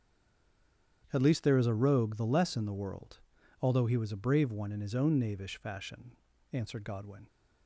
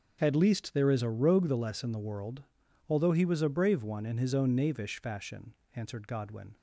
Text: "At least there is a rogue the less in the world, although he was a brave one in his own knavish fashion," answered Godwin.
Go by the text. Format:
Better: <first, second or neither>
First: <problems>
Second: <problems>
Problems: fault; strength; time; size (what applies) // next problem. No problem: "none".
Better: second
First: stays silent before the first word; until 1.0 s; 1.0 s long // starts louder than the rest; strong; until 2.1 s; 9 dB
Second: starts louder than the rest; until 1.2 s; 6.5 dB